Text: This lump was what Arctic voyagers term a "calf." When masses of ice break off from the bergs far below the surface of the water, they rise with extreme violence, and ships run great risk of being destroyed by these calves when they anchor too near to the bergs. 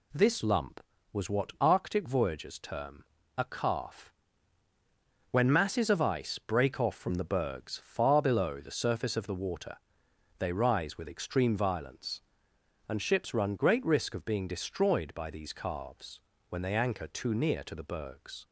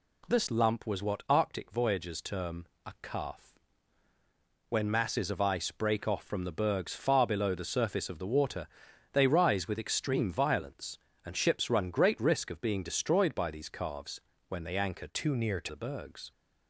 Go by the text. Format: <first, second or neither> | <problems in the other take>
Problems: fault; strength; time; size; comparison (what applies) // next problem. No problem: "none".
first | pauses between "term" and "a"; slight; at 2.6 s; 0.22 s long; slight in the first // pauses between "calves" and "when"; slight; at 14.1 s; 0.30 s long; slight in the first // changes voice from "too" to "to"; from 15.0 to 15.6 s; 0.6 s long